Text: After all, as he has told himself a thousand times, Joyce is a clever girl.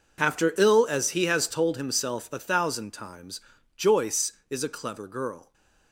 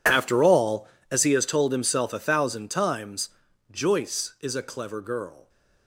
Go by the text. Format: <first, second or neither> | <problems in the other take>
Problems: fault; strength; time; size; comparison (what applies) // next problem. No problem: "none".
second | says "ill" for "all"; at 0.5 s